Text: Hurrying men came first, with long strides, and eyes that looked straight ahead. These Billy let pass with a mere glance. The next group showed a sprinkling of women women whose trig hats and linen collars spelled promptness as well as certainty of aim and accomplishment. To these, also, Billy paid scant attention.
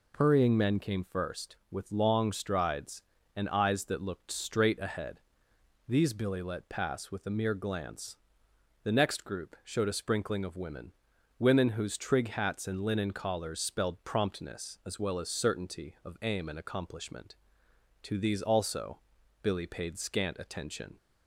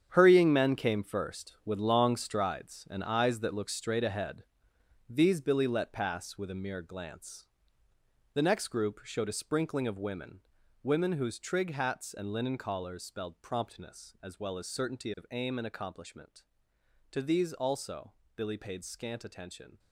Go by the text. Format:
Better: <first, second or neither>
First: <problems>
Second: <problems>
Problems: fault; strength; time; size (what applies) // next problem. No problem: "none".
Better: first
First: pauses between "women" and "women"; at 10.9 s; 0.44 s long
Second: gets quieter; strong; throughout; 11.5 dB // pauses between "women" and "women"; at 10.3 s; 0.42 s long